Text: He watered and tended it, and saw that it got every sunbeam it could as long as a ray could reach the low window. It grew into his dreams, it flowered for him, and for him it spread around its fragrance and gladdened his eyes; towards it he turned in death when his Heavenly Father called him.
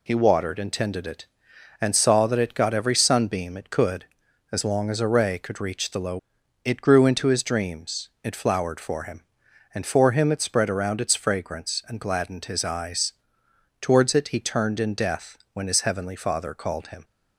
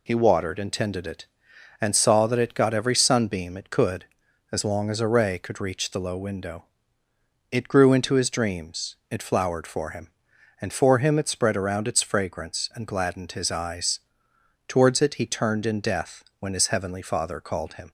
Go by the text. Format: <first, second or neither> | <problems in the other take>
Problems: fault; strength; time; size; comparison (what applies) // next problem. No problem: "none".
second | skips "window"; at 6.4 s // pauses between "death" and "when"; slight; at 15.3 s; 0.16 s long; slight in the second